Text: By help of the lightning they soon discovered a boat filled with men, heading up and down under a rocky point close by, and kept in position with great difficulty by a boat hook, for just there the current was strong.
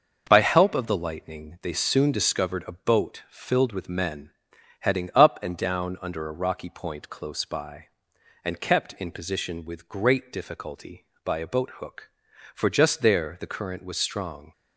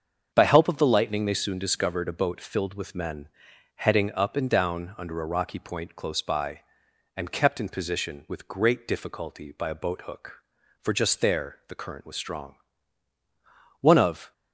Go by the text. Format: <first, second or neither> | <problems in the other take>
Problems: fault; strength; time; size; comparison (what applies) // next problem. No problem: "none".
first | starts louder than the rest; until 1.3 s; 7 dB; noticeable in the first // goes on to say "One of"; from 13.8 s on; 0.52 s long